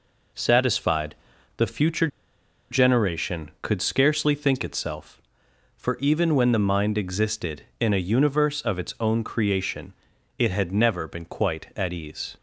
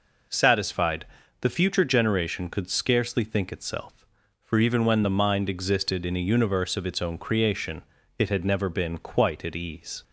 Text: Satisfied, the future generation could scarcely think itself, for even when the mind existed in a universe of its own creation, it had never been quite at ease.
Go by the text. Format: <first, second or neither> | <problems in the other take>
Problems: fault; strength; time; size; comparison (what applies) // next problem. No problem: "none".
second | pauses between "future" and "generation"; noticeable; at 2.0 s; 0.63 s long